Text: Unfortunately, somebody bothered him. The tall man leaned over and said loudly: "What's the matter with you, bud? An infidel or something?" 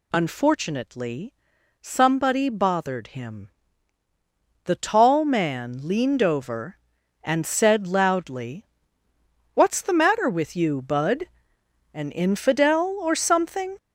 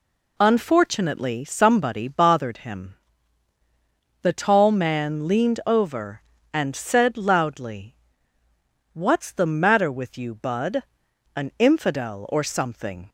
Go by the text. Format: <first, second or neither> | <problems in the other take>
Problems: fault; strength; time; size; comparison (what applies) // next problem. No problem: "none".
second | gets louder; throughout; 6.5 dB